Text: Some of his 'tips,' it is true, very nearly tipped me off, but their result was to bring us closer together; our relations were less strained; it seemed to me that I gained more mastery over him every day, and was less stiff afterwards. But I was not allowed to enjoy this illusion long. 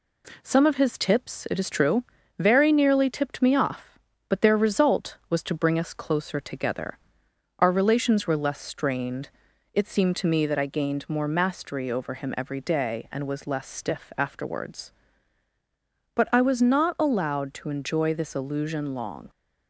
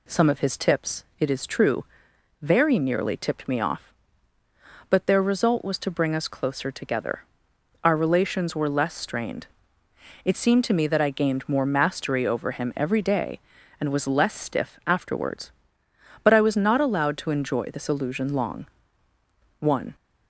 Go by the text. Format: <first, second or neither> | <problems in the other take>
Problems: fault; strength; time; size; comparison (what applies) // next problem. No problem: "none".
first | goes on to say "One"; slight; from 19.5 s on; 0.36 s long